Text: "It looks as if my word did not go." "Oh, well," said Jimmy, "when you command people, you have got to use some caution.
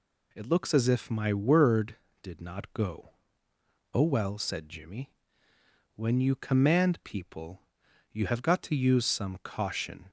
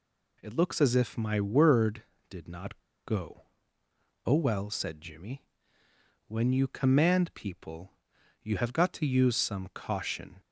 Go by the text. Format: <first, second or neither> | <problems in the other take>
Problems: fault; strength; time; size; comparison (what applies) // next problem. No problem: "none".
first | pauses between "not" and "go"; slight; at 2.7 s; 0.25 s long